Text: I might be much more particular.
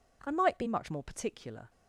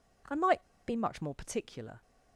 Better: first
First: none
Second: pauses between "might" and "be"; slight; at 0.6 s; 0.26 s long

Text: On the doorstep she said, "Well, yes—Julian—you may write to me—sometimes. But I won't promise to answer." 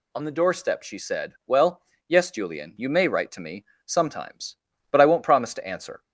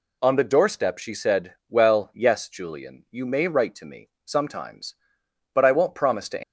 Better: first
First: none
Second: stops before "answer"; at 6.4 s

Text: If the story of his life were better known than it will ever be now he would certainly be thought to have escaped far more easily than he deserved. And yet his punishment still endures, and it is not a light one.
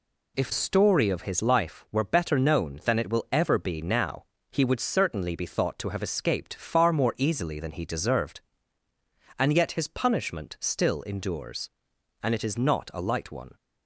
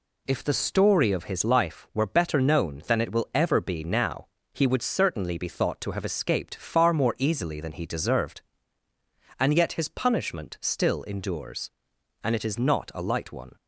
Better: second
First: skips "the"; at 0.5 s // pauses between "now" and "he"; slight; at 4.2 s; 0.28 s long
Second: pauses between "now" and "he"; slight; at 4.2 s; 0.28 s long

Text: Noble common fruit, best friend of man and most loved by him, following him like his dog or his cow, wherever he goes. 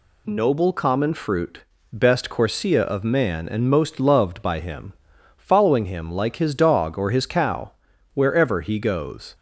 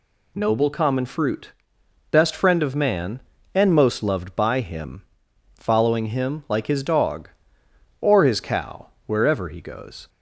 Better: second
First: says "corsia" for "friend"; at 2.2 s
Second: none

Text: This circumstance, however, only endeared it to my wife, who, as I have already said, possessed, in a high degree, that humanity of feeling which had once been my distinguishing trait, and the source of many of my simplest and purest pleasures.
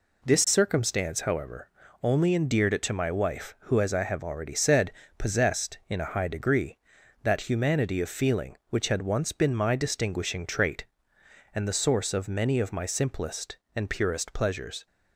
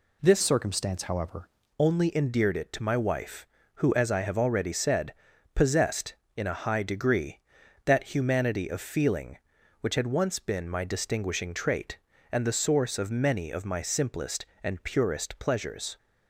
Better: first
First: none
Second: changes voice from "circumstance" to "however"; from 0.4 to 1.4 s; 1.0 s long

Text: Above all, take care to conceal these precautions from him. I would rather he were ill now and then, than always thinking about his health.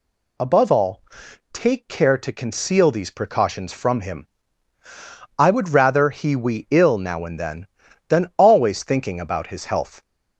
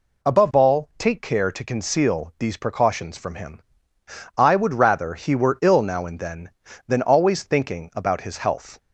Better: second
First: says "we" for "were"; at 6.3 s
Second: none

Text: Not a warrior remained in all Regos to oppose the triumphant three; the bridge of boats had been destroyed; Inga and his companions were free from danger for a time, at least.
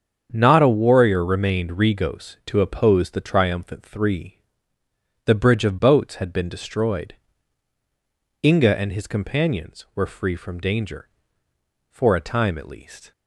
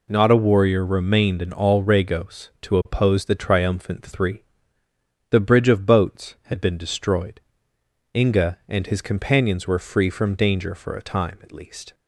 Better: second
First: starts louder than the rest; strong; until 1.3 s; 7.5 dB // skips "in all"; at 1.7 s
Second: none

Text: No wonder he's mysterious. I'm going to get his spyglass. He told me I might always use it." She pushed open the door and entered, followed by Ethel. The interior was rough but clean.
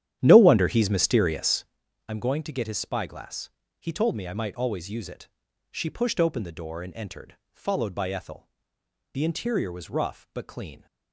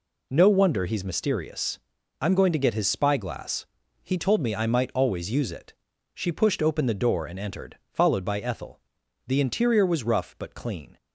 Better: second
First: starts louder than the rest; strong; until 1.8 s; 10.5 dB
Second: none

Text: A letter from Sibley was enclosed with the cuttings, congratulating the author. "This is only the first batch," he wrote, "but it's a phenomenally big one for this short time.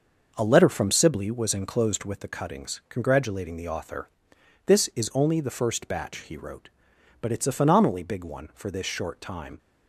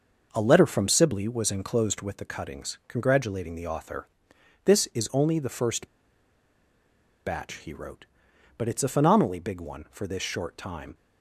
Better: first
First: starts louder than the rest; until 1.3 s; 6 dB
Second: starts louder than the rest; until 1.3 s; 6 dB // pauses between "first" and "batch"; strong; at 5.8 s; 1.3 s long

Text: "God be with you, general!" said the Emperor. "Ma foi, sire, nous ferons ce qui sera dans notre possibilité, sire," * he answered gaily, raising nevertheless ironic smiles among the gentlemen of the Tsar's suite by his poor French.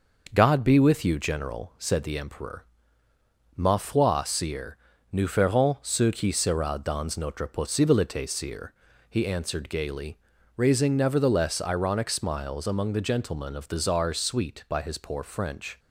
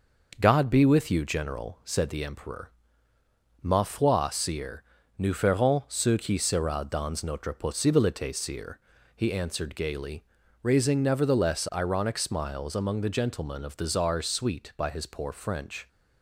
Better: neither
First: none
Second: none

